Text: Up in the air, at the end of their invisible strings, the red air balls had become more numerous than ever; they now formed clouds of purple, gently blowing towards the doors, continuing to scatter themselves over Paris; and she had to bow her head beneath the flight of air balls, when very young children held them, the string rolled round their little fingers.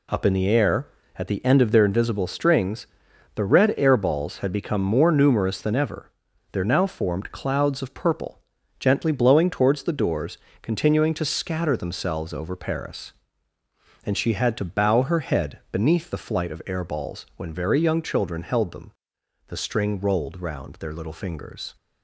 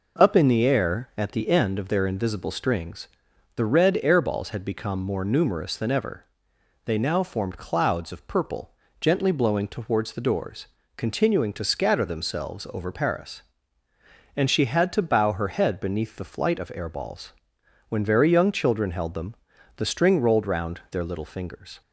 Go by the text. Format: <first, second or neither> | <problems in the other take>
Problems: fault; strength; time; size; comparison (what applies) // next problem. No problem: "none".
second | says "there" for "they"; at 6.5 s